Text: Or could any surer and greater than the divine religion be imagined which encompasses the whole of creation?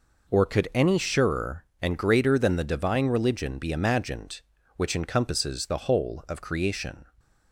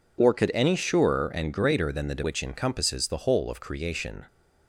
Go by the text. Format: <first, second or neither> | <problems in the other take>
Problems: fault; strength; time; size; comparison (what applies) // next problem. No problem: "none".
first | skips "divine religion be imagined"; at 2.2 s